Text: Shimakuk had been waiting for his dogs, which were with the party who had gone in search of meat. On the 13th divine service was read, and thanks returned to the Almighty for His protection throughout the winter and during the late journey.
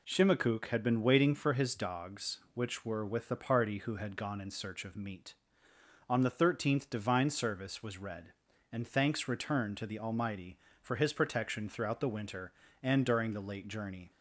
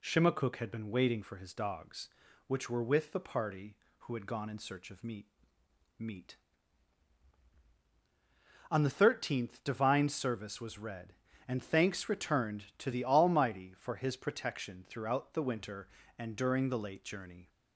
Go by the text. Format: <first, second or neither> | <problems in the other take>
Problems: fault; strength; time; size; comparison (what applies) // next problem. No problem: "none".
first | says "meat" twice; at 5.9 s